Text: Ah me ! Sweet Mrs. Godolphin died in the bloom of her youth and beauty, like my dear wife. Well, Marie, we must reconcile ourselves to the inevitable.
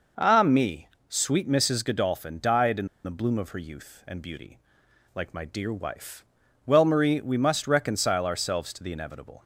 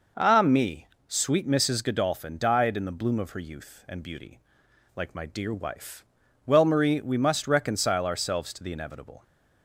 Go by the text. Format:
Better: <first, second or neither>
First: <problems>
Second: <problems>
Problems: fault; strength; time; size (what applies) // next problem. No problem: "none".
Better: second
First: pauses between "in" and "the"; slight; at 2.8 s; 0.18 s long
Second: none